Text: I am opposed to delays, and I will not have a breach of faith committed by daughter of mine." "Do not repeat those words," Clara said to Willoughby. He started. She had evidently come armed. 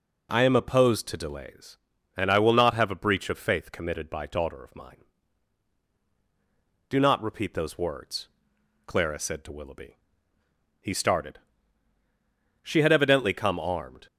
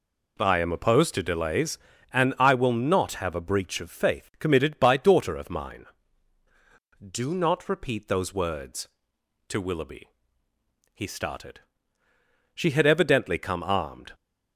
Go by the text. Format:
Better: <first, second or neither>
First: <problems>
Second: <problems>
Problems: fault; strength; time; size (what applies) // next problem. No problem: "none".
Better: first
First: none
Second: skips "Clara said"; at 9.1 s